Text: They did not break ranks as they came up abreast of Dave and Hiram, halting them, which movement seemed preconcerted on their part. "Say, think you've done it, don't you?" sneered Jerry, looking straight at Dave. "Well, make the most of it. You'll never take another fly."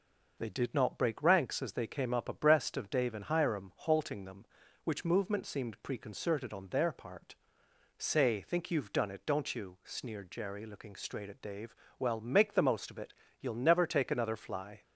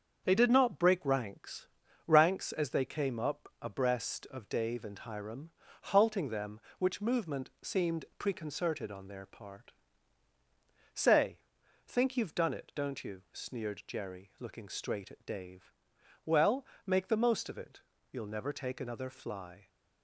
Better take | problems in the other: first | starts louder than the rest; until 1.2 s; 7 dB // says "ranks" twice; at 2.0 s

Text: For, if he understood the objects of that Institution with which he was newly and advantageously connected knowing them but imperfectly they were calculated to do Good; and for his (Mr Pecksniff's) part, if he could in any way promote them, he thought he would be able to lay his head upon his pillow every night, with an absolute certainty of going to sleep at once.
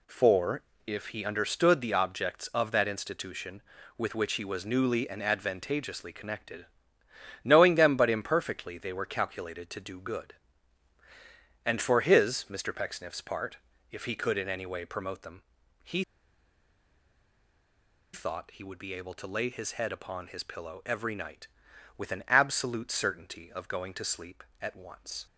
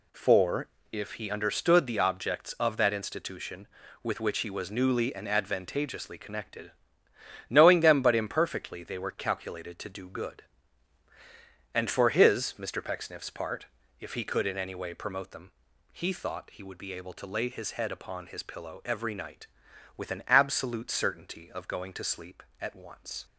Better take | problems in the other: second | pauses between "connected" and "knowing"; noticeable; at 6.6 s; 0.76 s long; noticeable in the second // pauses between "he" and "thought"; strong; at 16.0 s; 2.0 s long

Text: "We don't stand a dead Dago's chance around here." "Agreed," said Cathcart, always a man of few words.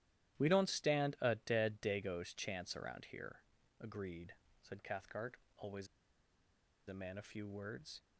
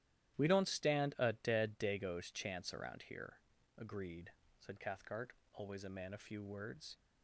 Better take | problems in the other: second | starts louder than the rest; strong; until 1.4 s; 12.5 dB; strong in the second // pauses between "always" and "a"; at 5.8 s; 1.0 s long

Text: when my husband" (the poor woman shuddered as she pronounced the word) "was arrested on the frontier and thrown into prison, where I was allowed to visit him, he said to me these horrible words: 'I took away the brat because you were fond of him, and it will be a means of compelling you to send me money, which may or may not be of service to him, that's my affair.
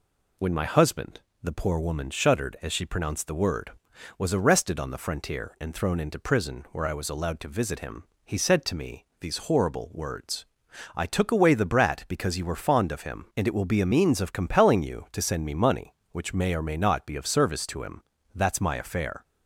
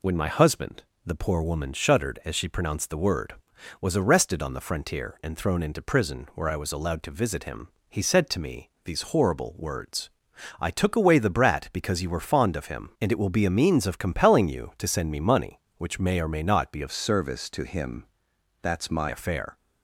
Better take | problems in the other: first | changes voice from "service" to "my"; from 16.9 to 19.0 s; 2.1 s long

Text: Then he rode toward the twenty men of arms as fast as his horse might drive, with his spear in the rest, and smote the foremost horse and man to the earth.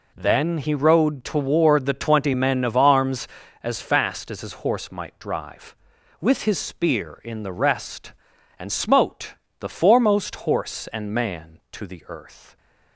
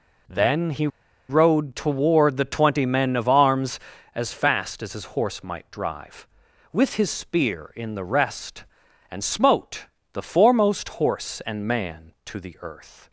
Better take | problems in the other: first | pauses between "he" and "rode"; at 0.8 s; 0.41 s long // pauses between "smote" and "the"; slight; at 9.8 s; 0.28 s long; slight in the first

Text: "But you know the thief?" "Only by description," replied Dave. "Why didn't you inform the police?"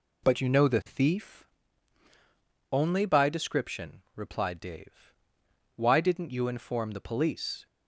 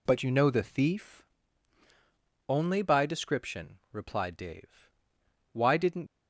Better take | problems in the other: first | stops before "you inform the police"; at 6.0 s

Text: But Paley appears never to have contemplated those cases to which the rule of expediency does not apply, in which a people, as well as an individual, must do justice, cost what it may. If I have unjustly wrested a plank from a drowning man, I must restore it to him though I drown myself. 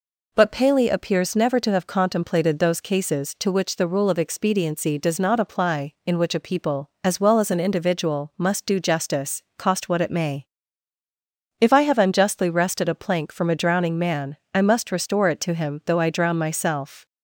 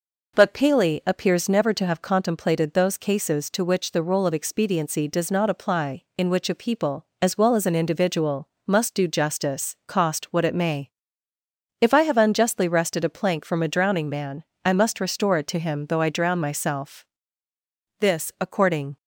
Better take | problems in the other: first | goes on to say "This according"; noticeable; from 17.9 s on; 0.98 s long

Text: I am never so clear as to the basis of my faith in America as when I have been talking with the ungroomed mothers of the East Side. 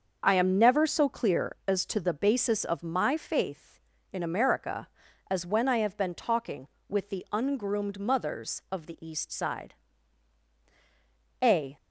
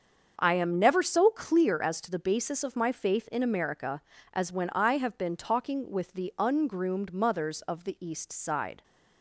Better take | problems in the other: second | starts louder than the rest; until 1.2 s; 6.5 dB; also in the second // goes on to say "A"; slight; from 11.4 s on; 0.34 s long

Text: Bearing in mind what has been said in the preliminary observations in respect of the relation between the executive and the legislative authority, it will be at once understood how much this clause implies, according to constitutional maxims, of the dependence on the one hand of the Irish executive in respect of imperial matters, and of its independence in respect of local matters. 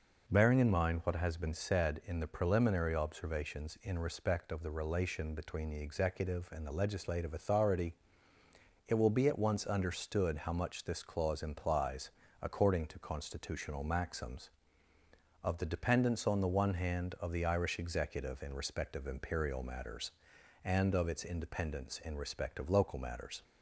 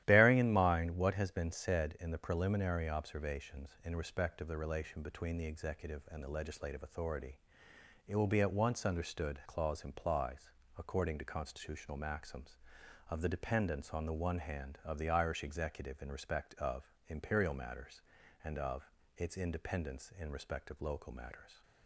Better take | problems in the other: first | starts louder than the rest; strong; until 1.0 s; 13 dB // skips "how much this"; at 9.4 s // pauses between "of" and "its"; slight; at 18.8 s; 0.30 s long

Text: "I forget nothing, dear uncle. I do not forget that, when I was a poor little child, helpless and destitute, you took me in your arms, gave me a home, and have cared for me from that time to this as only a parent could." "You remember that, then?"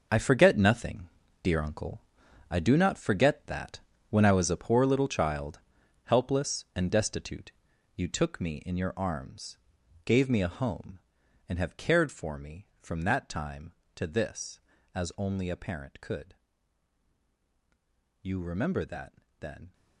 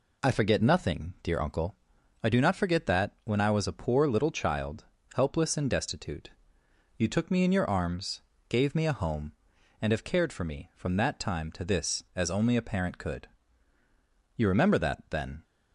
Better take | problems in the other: second | gets quieter; strong; throughout; 11 dB

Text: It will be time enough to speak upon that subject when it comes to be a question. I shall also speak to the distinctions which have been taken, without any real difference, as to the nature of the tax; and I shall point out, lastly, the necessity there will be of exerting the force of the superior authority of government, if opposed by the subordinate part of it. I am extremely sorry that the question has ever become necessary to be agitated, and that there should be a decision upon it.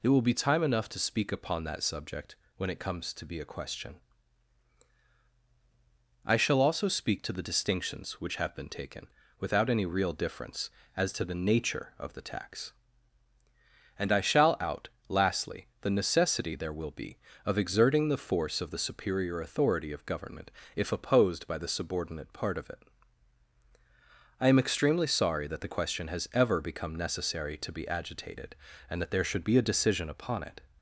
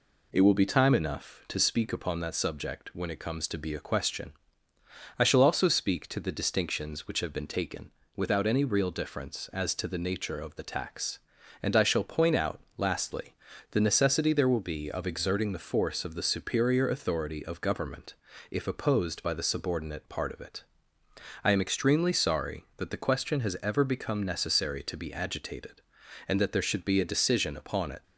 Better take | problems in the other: second | pauses between "subject" and "when"; slight; at 2.3 s; 0.22 s long // skips "point"; at 14.5 s

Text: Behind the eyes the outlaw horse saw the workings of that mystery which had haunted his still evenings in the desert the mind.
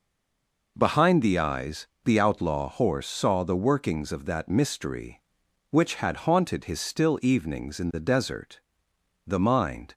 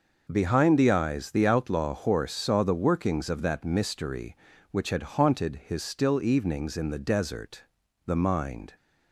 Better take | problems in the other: second | stays silent before the first word; slight; until 0.7 s; 0.7 s long // pauses between "eyes" and "the"; slight; at 1.8 s; 0.20 s long // pauses between "desert" and "the"; noticeable; at 8.5 s; 0.68 s long; also in the second

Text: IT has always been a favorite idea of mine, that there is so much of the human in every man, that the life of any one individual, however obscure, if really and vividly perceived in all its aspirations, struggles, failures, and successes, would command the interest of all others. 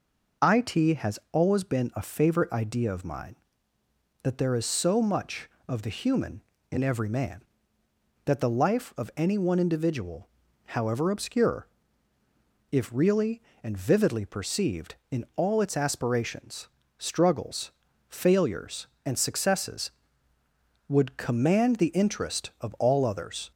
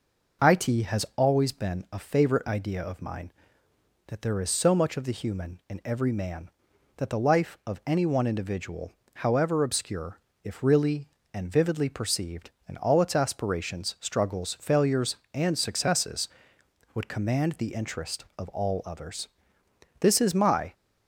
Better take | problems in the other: first | goes on to say "This is my"; noticeable; from 19.9 s on; 0.74 s long

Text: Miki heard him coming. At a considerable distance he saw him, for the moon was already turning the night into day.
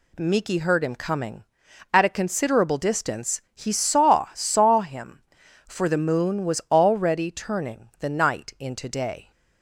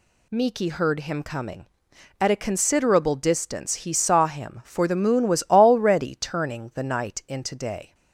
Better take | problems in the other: second | says "saw" twice; at 4.3 s

